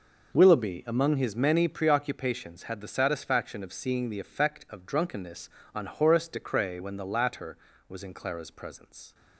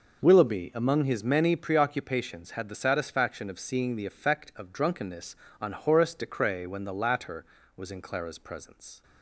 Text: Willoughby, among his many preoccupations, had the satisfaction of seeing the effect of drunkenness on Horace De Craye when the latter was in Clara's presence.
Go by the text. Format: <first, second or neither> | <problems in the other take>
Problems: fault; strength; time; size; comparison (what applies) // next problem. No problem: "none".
neither | none